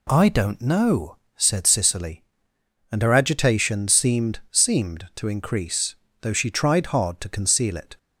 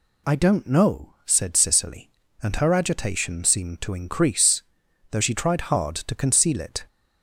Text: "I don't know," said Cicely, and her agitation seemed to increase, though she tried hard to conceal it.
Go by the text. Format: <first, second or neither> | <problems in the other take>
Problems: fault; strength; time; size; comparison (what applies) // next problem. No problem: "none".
second | says "seemed" twice; at 4.4 s